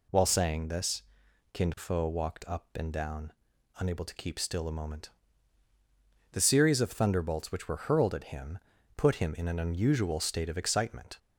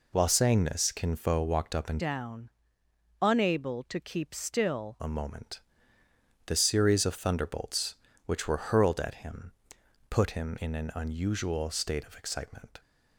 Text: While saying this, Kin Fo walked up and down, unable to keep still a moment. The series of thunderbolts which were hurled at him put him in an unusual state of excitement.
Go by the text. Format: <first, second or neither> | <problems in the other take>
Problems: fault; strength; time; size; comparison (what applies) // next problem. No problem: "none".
first | changes voice from "down" to "still"; from 1.9 to 4.9 s; 3.0 s long // pauses between "him" and "put"; noticeable; at 9.5 s; 0.58 s long; also in the first